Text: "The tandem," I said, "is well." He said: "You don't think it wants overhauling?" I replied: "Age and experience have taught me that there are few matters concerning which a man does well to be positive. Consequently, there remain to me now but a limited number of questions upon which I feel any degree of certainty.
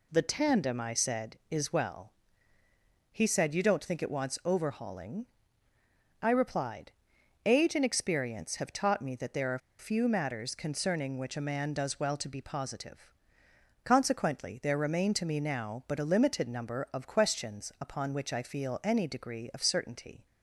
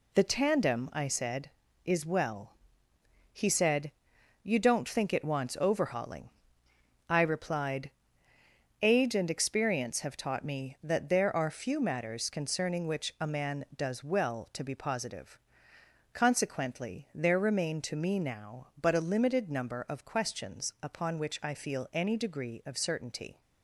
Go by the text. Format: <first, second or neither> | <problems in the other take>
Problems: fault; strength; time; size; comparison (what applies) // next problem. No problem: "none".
second | pauses between "are" and "few"; slight; at 9.5 s; 0.20 s long